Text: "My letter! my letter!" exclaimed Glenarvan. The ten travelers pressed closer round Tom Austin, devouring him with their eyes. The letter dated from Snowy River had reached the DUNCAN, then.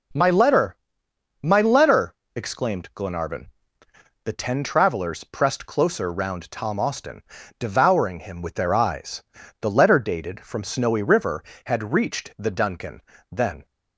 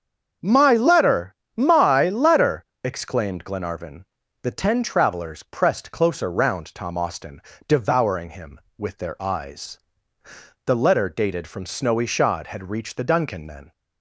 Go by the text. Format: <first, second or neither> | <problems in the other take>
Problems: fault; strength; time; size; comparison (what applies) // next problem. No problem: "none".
first | starts louder than the rest; until 1.6 s; 7 dB // says "Shod" for "River"; at 12.0 s